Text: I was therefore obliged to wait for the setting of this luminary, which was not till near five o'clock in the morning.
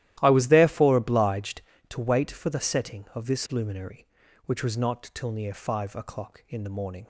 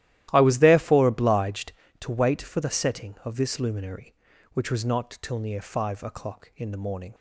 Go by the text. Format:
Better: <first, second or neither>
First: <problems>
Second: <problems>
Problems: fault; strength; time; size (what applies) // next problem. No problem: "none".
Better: neither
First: starts louder than the rest; strong; until 1.2 s; 14 dB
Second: starts louder than the rest; strong; until 1.3 s; 14 dB